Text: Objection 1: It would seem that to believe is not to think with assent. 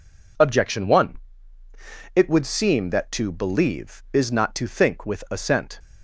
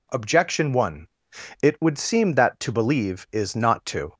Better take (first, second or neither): first